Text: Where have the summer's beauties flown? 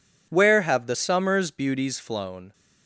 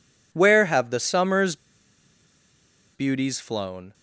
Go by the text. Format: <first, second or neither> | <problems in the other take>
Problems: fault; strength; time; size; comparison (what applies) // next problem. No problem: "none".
first | pauses between "summer's" and "beauties"; strong; at 1.5 s; 1.3 s long